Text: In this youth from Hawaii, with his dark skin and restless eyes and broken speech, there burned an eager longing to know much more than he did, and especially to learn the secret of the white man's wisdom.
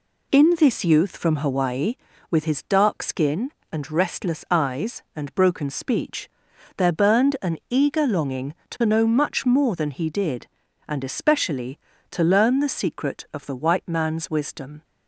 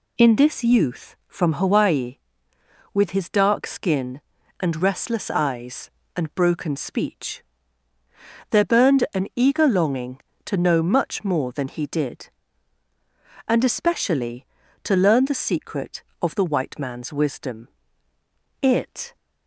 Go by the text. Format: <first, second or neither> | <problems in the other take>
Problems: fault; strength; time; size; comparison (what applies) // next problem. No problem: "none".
first | goes on to say "It"; from 18.6 s on; 0.54 s long